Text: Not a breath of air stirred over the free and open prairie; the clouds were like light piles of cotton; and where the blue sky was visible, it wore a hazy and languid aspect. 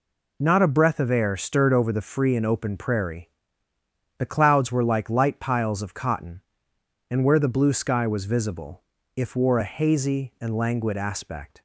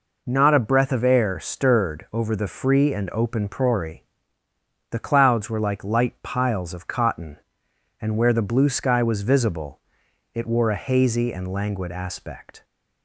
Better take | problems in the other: second | says "if" for "it"; at 9.1 s

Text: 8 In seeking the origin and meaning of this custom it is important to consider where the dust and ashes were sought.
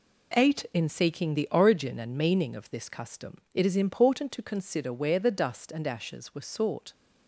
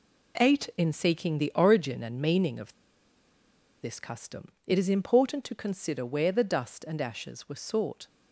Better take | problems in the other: first | pauses between "of" and "this"; at 2.7 s; 1.0 s long // pauses between "custom" and "it"; slight; at 4.4 s; 0.16 s long

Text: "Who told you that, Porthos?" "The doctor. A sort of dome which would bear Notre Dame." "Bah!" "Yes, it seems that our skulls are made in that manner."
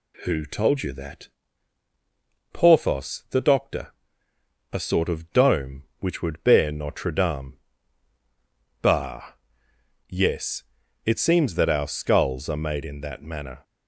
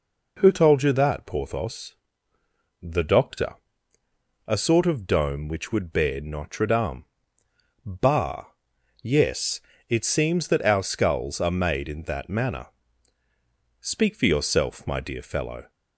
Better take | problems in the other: first | goes on to say "Speak for yourself my dear fellow"; strong; from 13.7 s on; 1.9 s long

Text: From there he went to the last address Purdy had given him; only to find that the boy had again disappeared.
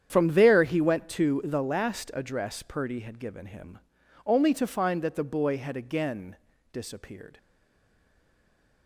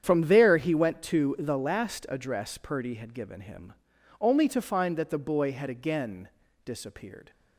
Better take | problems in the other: second | starts louder than the rest; strong; until 1.1 s; 8.5 dB; strong in the second // pauses between "again" and "disappeared"; slight; at 6.3 s; 0.36 s long; slight in the second // stays silent after the last word; noticeable; from 7.3 s on; 1.5 s long

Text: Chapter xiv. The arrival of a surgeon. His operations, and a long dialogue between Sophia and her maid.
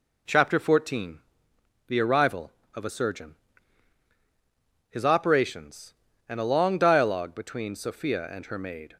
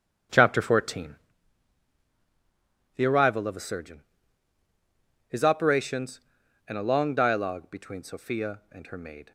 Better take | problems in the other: first | starts louder than the rest; until 1.3 s; 7 dB

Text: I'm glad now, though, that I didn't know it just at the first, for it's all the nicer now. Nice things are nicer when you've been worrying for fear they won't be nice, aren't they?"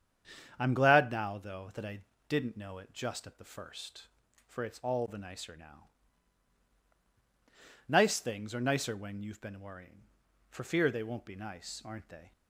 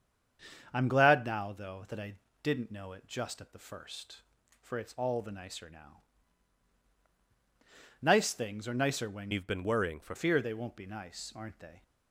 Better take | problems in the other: first | starts louder than the rest; strong; until 1.7 s; 7.5 dB; strong in the first // pauses between "I" and "didn't"; slight; at 2.1 s; 0.28 s long; slight in the first // changes voice from "you've" to "for"; from 9.3 to 10.1 s; 0.8 s long

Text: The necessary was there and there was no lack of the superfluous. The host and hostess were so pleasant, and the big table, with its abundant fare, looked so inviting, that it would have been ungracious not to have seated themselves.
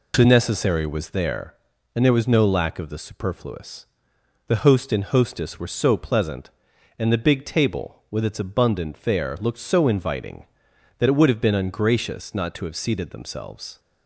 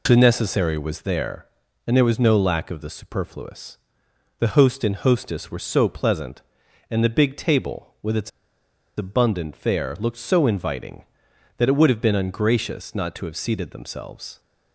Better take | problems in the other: first | pauses between "its" and "abundant"; noticeable; at 8.3 s; 0.67 s long

